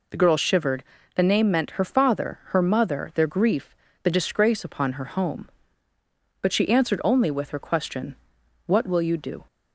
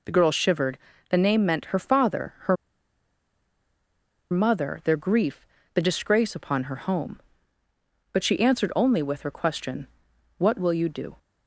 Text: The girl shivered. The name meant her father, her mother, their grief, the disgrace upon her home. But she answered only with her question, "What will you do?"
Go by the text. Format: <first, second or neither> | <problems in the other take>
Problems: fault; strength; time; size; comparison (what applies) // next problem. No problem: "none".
first | pauses between "her" and "mother"; strong; at 2.5 s; 1.7 s long